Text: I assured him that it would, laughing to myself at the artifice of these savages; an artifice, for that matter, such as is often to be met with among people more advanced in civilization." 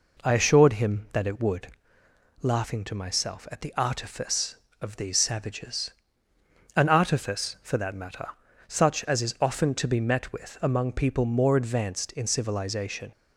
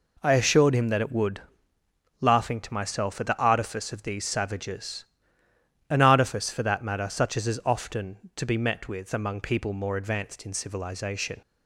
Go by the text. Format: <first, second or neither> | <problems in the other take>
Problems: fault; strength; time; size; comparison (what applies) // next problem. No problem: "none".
neither | none